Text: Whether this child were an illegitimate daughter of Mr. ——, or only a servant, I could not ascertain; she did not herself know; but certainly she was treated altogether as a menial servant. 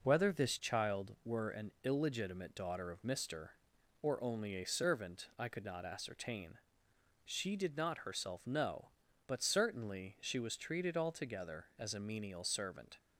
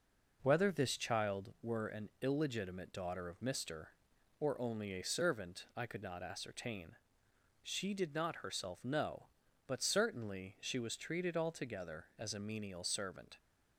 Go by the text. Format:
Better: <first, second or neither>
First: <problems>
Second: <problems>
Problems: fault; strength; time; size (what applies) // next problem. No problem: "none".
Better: neither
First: none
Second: none